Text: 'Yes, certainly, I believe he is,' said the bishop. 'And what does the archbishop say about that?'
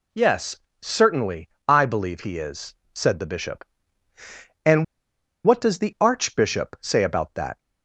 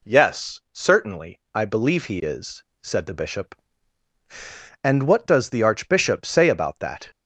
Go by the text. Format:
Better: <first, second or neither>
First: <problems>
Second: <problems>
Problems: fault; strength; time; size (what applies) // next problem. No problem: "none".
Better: second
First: pauses between "And" and "what"; noticeable; at 4.8 s; 0.60 s long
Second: none